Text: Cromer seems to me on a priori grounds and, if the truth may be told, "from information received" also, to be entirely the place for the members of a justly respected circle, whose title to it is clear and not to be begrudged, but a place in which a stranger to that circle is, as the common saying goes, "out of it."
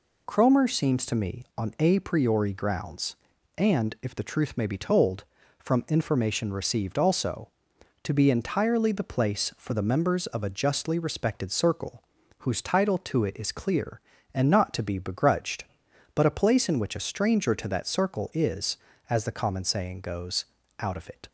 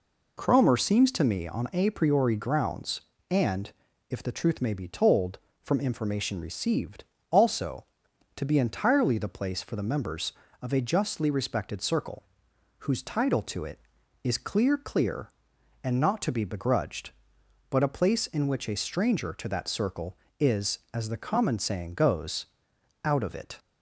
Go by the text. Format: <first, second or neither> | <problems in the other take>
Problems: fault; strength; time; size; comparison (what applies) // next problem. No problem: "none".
first | pauses between "received" and "also"; slight; at 7.0 s; 0.26 s long // says "clear" twice; at 14.7 s